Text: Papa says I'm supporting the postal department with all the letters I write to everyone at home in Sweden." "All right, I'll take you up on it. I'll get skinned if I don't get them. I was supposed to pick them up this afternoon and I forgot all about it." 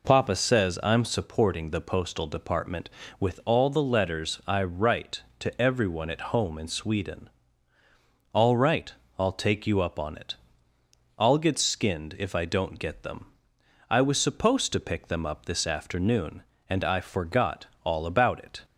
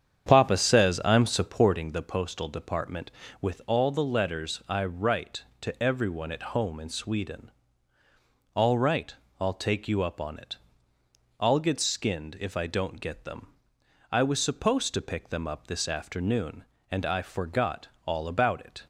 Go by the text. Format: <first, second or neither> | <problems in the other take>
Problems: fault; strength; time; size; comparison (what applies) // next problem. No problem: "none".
first | starts louder than the rest; strong; until 2.0 s; 8.5 dB // pauses between "forgot" and "all"; slight; at 17.8 s; 0.18 s long; slight in the first